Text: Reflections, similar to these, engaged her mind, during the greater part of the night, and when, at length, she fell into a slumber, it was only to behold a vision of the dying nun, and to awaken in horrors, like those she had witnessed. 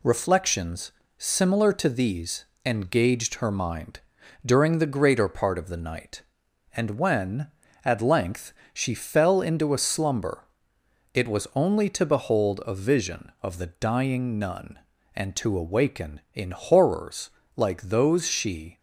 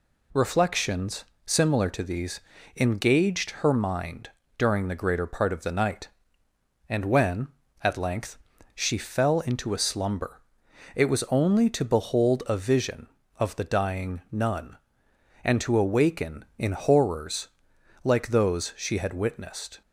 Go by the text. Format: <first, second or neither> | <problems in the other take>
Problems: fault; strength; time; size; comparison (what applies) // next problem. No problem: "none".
second | stops before "had witnessed"; at 18.7 s